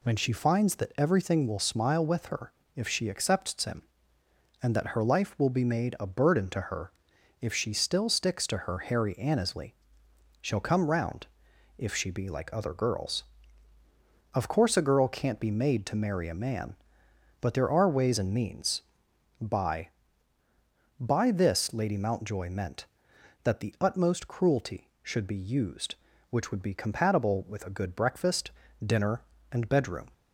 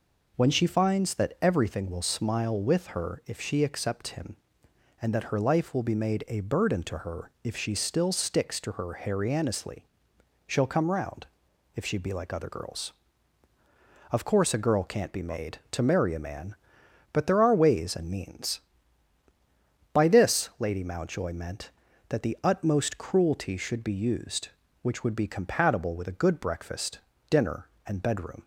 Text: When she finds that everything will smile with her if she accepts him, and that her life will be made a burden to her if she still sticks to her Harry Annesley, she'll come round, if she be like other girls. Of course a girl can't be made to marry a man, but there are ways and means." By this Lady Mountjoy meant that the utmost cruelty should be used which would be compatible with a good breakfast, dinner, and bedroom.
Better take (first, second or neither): second